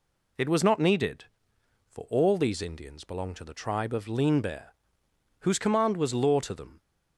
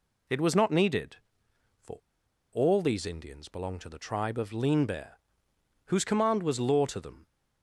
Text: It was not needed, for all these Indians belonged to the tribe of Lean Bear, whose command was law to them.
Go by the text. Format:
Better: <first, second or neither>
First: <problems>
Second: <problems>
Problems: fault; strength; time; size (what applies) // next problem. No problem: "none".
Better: first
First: none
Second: pauses between "for" and "all"; noticeable; at 1.9 s; 0.56 s long